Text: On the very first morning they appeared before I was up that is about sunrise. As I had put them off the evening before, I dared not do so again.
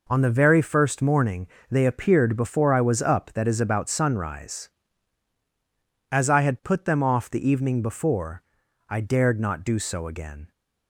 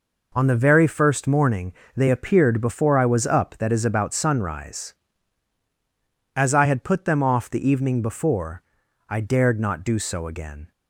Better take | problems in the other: neither | pauses between "morning" and "they"; slight; the same in both

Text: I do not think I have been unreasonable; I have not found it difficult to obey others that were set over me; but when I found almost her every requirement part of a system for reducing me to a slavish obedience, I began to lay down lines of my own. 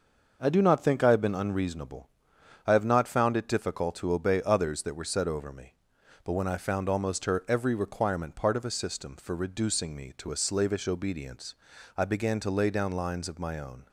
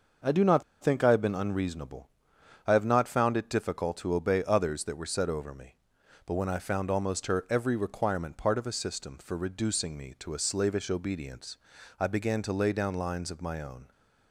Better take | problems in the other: first | pauses between "not" and "think"; slight; at 0.6 s; 0.19 s long

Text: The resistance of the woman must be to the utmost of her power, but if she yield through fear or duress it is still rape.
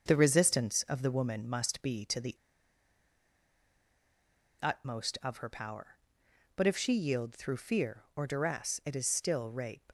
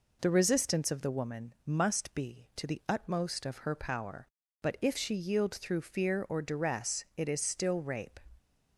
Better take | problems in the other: second | starts louder than the rest; until 1.0 s; 6.5 dB // pauses between "the" and "utmost"; strong; at 2.3 s; 2.2 s long

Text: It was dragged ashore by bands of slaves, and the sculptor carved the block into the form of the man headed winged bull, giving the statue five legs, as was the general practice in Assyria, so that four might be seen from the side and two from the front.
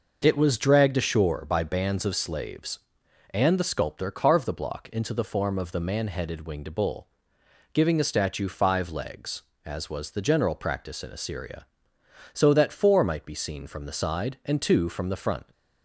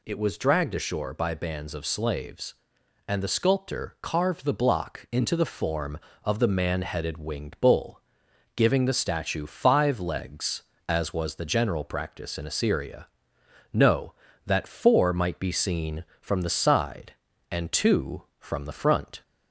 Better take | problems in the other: first | says "no" for "so"; at 13.7 s

